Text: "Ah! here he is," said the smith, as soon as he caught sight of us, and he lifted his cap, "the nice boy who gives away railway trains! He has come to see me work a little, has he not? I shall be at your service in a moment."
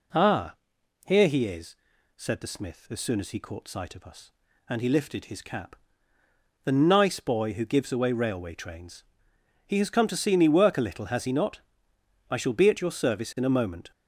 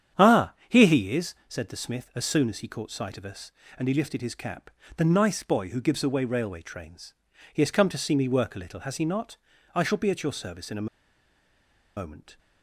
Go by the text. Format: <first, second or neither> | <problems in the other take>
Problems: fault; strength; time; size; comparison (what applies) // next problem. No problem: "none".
first | starts louder than the rest; strong; until 1.3 s; 9 dB // pauses between "a" and "moment"; at 10.8 s; 1.0 s long